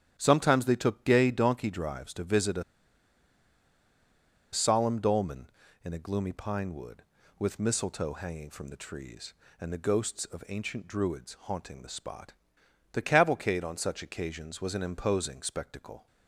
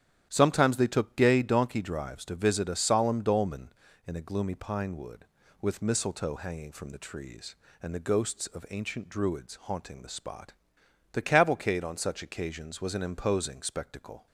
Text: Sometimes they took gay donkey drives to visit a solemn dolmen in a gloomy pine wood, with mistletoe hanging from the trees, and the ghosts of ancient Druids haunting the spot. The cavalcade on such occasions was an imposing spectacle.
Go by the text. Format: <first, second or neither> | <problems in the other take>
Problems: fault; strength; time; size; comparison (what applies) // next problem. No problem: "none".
second | starts louder than the rest; strong; until 1.1 s; 10.5 dB; strong in the second // pauses between "a" and "solemn"; strong; at 2.6 s; 1.8 s long